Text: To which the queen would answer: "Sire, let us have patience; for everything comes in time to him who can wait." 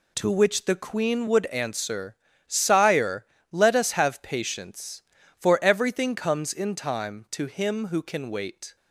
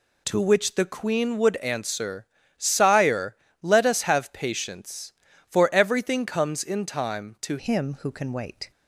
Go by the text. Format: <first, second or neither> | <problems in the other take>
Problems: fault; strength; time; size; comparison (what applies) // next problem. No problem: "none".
first | changes voice at "him"; from 7.5 s on; 1.2 s long